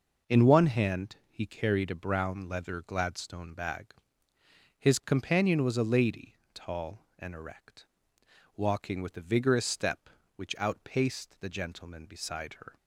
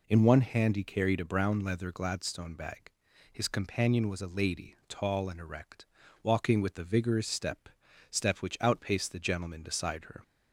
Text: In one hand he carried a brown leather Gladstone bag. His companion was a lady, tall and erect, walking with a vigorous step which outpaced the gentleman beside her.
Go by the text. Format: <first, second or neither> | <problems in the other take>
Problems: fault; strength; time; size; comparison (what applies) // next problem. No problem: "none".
first | says "step" twice; at 8.1 s